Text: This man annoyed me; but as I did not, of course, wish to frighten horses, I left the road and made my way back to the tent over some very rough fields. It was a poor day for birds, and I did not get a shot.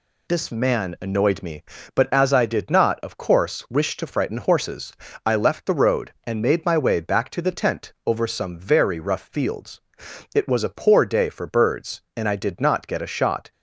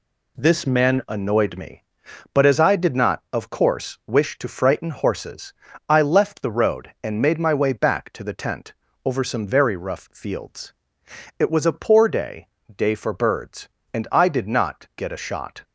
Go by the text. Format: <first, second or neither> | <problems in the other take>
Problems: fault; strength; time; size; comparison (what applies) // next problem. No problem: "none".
first | pauses between "tent" and "over"; slight; at 8.7 s; 0.32 s long // says "day" twice; at 12.7 s